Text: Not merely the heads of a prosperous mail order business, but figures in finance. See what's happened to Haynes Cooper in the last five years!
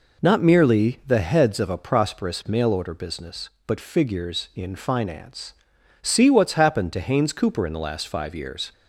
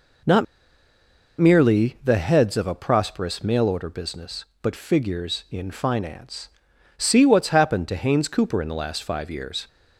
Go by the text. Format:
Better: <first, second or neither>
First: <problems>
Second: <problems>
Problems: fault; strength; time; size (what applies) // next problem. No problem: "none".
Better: first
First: none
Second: pauses between "Not" and "merely"; noticeable; at 0.4 s; 0.94 s long